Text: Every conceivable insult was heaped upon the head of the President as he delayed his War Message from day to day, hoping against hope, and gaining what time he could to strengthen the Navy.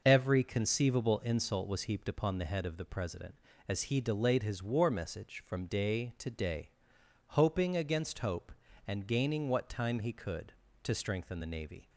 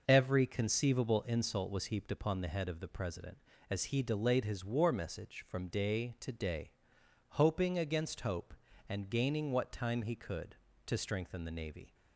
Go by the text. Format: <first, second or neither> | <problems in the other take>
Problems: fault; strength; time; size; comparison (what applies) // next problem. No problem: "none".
neither | none